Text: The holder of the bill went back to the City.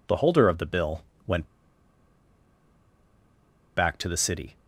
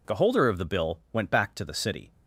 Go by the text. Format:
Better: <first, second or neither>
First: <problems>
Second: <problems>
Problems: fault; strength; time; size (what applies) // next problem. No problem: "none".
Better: second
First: pauses between "bill" and "went"; slight; at 1.0 s; 0.24 s long // pauses between "went" and "back"; strong; at 1.4 s; 2.3 s long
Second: none